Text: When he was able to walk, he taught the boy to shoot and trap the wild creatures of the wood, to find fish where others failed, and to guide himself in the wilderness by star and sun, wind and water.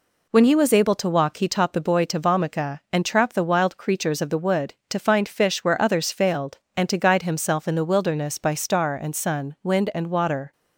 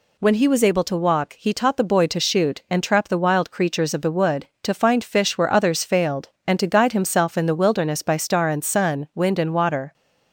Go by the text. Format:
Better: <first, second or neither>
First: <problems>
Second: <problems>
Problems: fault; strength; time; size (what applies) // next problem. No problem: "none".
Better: second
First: says "vomica" for "shoot"; at 2.1 s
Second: none